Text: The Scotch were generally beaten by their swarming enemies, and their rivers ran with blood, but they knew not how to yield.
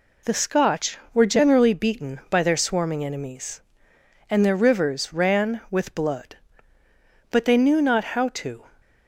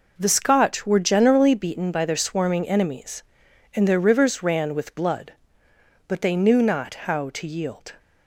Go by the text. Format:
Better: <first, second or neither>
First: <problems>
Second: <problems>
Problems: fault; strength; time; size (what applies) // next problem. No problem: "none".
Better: second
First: stops before "yield"; at 8.8 s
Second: none